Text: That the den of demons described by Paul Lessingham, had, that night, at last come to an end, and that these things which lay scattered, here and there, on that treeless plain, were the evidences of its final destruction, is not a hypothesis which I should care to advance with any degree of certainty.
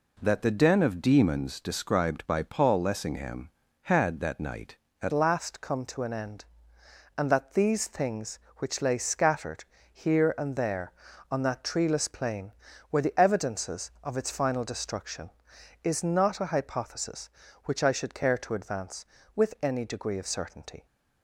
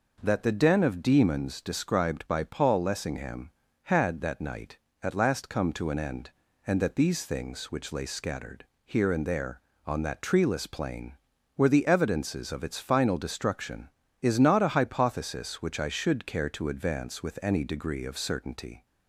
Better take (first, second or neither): second